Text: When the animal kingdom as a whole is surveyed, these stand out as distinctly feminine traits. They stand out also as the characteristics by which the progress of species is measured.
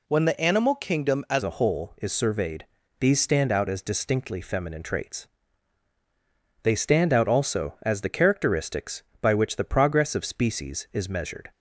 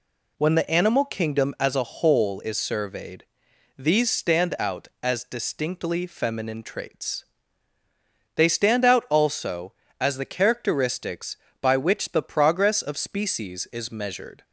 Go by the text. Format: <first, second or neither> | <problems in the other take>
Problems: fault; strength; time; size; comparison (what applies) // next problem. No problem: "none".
second | changes voice at "a"; from 1.4 s on; 10.1 s long